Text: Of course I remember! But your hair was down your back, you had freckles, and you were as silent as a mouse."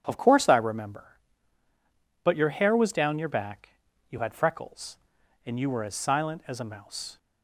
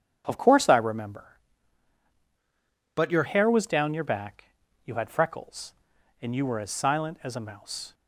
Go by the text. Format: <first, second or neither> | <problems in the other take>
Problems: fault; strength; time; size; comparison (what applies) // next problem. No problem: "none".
first | starts louder than the rest; strong; until 1.2 s; 9.5 dB; strong in the first // changes voice from "But" to "your"; from 2.9 to 3.2 s; 0.3 s long